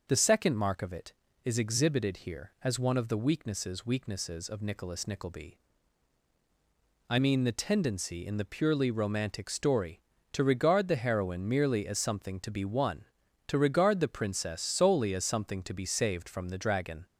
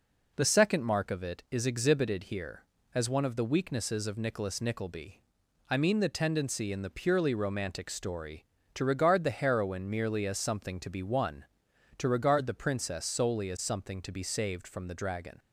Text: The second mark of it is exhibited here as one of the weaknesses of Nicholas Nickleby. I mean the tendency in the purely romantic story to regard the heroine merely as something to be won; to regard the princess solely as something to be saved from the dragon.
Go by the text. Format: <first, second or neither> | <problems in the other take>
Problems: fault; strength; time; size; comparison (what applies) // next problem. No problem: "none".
second | says "weaknesses" twice; at 3.8 s